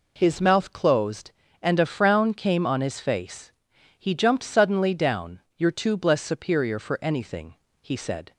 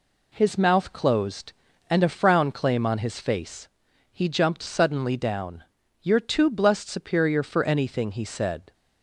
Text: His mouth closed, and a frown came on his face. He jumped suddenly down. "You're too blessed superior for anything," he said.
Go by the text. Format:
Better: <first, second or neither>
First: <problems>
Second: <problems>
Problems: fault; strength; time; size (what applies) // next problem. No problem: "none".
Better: first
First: none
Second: says "claim" for "came"; at 2.5 s